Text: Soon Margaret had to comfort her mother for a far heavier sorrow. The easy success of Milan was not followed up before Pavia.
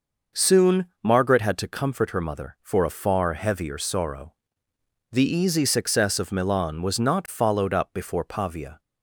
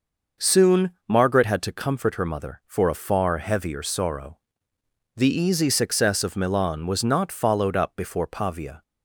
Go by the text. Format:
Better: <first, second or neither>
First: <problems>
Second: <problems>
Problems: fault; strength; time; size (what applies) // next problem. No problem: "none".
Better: neither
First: pauses between "Soon" and "Margaret"; slight; at 0.8 s; 0.18 s long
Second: pauses between "Soon" and "Margaret"; slight; at 0.9 s; 0.18 s long